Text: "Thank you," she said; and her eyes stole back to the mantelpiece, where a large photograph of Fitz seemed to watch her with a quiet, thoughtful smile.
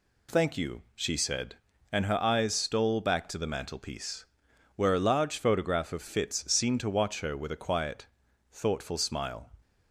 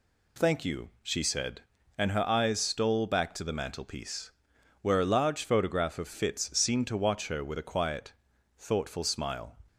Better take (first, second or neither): neither